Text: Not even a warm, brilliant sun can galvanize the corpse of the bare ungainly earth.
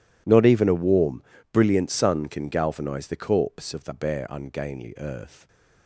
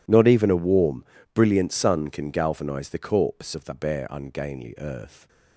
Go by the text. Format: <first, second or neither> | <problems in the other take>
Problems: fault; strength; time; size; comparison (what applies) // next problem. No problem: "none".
neither | none